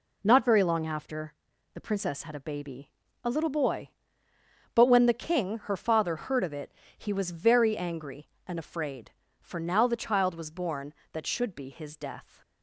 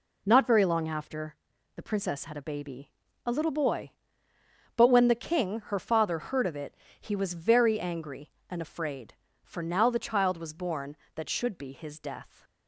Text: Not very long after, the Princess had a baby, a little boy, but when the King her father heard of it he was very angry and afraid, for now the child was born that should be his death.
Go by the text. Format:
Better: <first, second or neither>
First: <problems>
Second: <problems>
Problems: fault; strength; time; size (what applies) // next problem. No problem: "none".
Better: neither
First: pauses between "it" and "he"; slight; at 6.7 s; 0.26 s long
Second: pauses between "it" and "he"; slight; at 6.7 s; 0.26 s long